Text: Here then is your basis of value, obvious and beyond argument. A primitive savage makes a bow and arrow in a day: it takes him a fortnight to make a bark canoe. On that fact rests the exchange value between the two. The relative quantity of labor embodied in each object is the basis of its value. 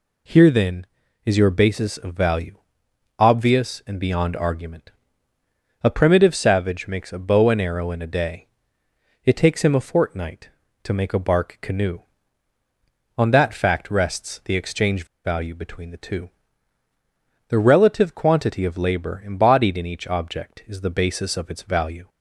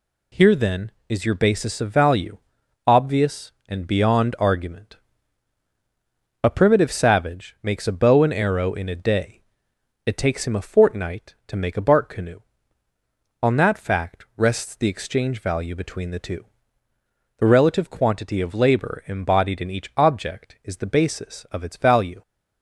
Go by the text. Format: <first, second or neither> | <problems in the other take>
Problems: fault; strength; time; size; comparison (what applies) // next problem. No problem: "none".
second | pauses between "exchange" and "value"; slight; at 15.0 s; 0.18 s long